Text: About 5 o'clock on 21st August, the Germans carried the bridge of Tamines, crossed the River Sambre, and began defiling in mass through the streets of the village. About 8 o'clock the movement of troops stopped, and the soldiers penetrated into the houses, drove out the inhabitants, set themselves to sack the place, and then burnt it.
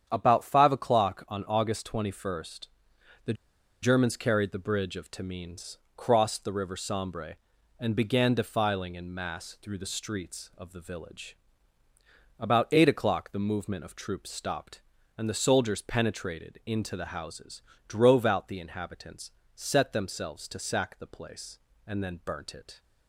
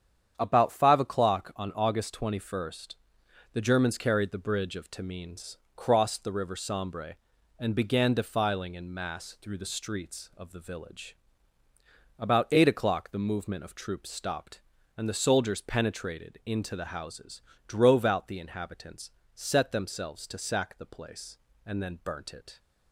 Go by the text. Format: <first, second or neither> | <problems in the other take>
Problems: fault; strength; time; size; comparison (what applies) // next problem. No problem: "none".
second | starts louder than the rest; strong; until 1.0 s; 8.5 dB; strong in the second // pauses between "the" and "Germans"; noticeable; at 3.3 s; 0.49 s long